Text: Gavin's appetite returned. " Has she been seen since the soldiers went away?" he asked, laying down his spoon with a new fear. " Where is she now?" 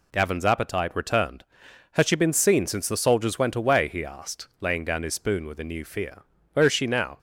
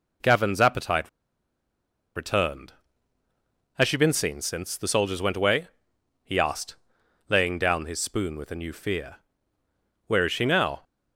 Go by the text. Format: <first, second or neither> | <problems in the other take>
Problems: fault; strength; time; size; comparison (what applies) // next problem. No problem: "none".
first | pauses between "appetite" and "returned"; at 1.0 s; 1.0 s long